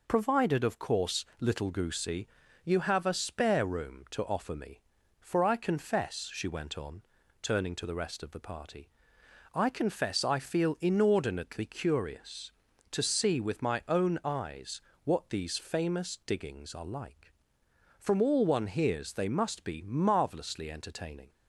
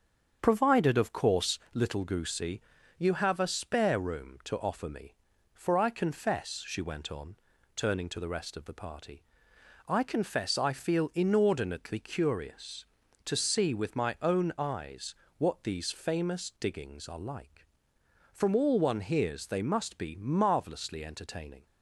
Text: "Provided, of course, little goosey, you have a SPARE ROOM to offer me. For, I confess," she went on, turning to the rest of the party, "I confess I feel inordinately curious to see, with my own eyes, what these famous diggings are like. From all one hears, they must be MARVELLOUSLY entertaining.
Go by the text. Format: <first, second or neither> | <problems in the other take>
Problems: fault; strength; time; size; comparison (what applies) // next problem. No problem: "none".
first | starts louder than the rest; strong; until 1.7 s; 7.5 dB